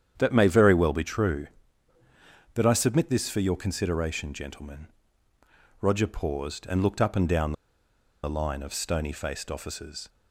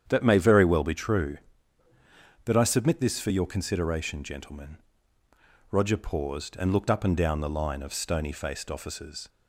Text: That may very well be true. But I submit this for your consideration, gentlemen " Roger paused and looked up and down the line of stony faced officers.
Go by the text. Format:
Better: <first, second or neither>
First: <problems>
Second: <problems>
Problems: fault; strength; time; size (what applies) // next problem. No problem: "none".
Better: second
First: starts louder than the rest; strong; until 1.1 s; 9 dB // pauses between "down" and "the"; noticeable; at 7.5 s; 0.71 s long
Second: starts louder than the rest; strong; until 1.0 s; 9 dB